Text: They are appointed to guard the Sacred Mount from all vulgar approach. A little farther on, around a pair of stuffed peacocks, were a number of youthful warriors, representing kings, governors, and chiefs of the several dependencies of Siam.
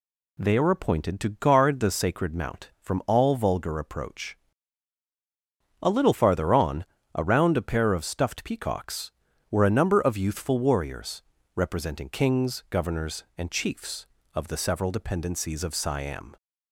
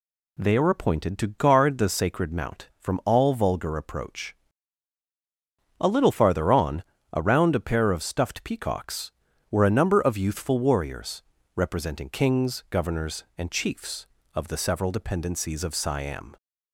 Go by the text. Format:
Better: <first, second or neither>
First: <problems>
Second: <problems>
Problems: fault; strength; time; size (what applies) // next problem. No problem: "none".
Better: neither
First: none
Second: none